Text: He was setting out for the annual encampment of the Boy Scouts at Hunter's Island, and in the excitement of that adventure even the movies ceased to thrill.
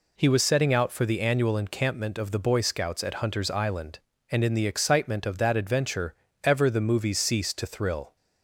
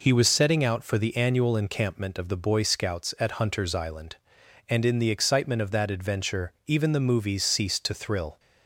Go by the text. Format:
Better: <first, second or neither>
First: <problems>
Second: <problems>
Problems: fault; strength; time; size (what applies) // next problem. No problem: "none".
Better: second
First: says "ever" for "even"; at 6.4 s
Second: none